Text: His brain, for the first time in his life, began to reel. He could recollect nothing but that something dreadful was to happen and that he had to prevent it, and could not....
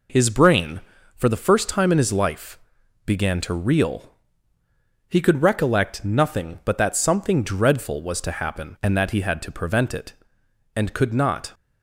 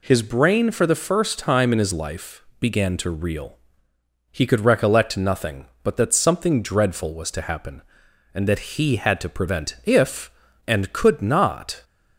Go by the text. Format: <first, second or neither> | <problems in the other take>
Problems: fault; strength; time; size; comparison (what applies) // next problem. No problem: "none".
first | says "if" for "it"; at 9.8 s